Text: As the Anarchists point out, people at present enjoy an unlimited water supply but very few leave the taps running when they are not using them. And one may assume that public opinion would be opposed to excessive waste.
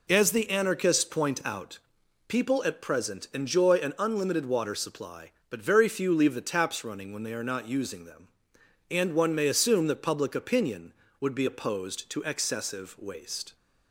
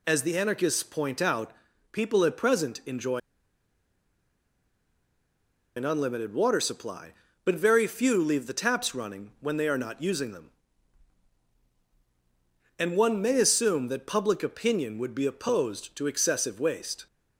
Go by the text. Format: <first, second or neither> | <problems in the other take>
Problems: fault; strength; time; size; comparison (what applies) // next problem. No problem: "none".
first | pauses between "enjoy" and "an"; strong; at 3.1 s; 2.5 s long